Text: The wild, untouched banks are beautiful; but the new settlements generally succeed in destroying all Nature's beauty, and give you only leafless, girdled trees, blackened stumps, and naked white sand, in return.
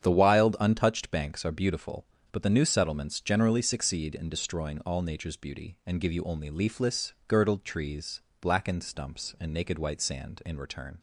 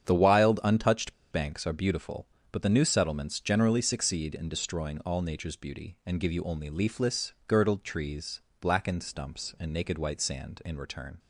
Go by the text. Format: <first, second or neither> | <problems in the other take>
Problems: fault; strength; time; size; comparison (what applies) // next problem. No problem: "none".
first | starts louder than the rest; strong; until 1.0 s; 8.5 dB; strong in the first // pauses between "untouched" and "banks"; slight; at 1.1 s; 0.20 s long